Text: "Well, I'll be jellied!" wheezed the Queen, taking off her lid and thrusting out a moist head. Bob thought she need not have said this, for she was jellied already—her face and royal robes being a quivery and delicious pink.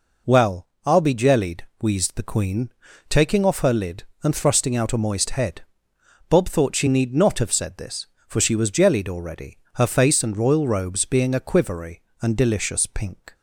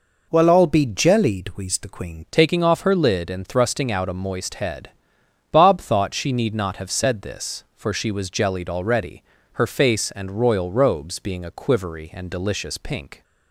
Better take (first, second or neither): first